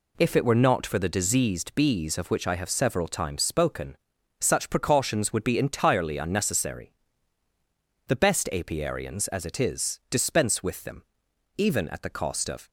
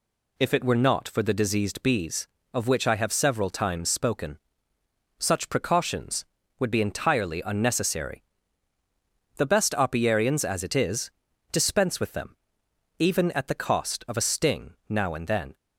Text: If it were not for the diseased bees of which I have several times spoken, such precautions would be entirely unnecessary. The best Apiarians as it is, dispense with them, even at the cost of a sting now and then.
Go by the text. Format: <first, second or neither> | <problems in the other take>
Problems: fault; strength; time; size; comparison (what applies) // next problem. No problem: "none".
second | stops before "a sting now and then"; at 12.6 s